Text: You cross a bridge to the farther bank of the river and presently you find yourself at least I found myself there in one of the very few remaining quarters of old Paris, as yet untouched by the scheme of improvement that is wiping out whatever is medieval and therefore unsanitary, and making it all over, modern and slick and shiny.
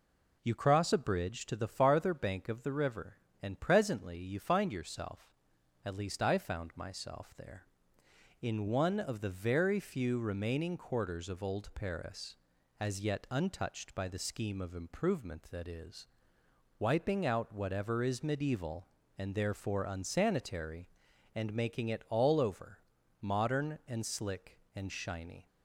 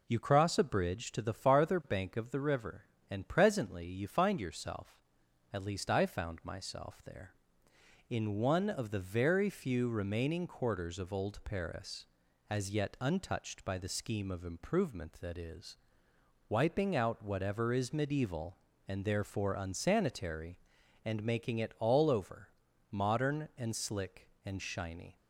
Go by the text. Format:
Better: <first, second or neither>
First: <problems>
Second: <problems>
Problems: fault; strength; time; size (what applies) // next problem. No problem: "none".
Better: neither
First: pauses between "is" and "wiping"; noticeable; at 16.0 s; 0.72 s long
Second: pauses between "is" and "wiping"; noticeable; at 15.7 s; 0.72 s long